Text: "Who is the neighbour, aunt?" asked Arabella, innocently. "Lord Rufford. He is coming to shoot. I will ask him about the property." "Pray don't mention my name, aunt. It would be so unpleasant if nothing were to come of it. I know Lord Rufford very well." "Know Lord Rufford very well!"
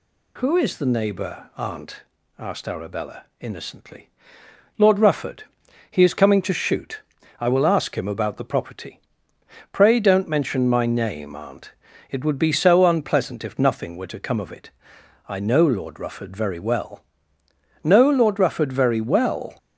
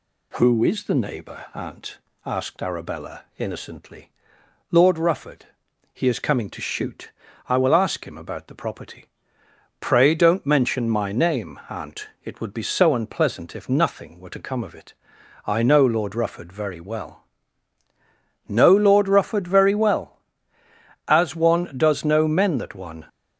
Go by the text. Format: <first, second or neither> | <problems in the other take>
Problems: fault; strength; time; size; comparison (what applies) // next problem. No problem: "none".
first | goes on to say "As one does know men that one"; strong; from 21.0 s on; 1.9 s long